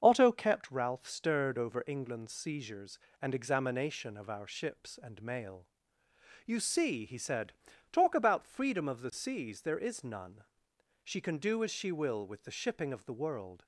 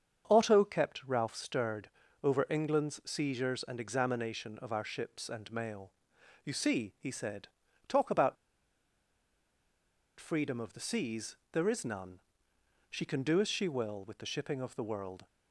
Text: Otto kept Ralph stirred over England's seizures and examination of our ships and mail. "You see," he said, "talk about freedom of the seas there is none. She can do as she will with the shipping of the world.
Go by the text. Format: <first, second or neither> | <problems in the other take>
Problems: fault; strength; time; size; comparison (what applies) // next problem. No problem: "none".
first | starts louder than the rest; strong; until 1.3 s; 7 dB; also in the first // pauses between "stirred" and "over"; slight; at 1.8 s; 0.36 s long // pauses between "about" and "freedom"; strong; at 8.3 s; 1.8 s long // pauses between "seas" and "there"; slight; at 11.3 s; 0.16 s long